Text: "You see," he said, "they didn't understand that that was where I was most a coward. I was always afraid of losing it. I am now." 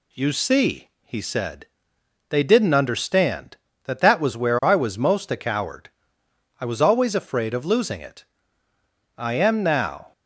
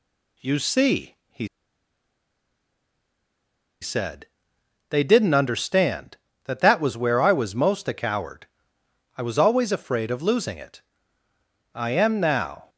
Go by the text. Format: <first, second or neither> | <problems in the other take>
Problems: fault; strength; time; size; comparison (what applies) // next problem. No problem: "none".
first | pauses between "he" and "said"; strong; at 1.4 s; 2.3 s long